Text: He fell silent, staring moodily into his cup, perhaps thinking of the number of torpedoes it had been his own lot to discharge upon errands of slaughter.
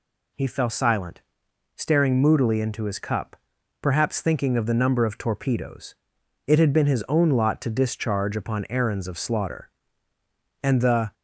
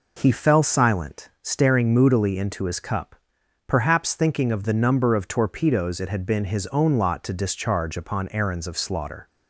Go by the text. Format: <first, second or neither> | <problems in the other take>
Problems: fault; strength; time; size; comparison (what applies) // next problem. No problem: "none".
second | pauses between "torpedoes" and "it"; noticeable; at 5.9 s; 0.50 s long // goes on to say "And the"; from 10.6 s on; 0.52 s long